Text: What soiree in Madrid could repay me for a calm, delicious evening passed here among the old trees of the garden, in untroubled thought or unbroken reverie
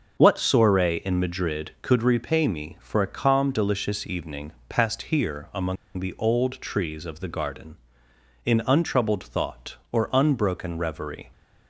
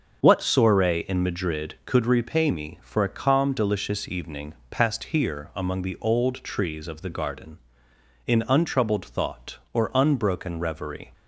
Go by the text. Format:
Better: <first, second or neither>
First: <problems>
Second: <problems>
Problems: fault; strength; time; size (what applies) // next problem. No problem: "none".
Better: second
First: starts louder than the rest; until 1.2 s; 6.5 dB // pauses between "evening" and "passed"; slight; at 4.5 s; 0.18 s long // pauses between "among" and "the"; slight; at 5.7 s; 0.21 s long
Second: starts louder than the rest; until 1.2 s; 6.5 dB // pauses between "evening" and "passed"; slight; at 4.5 s; 0.18 s long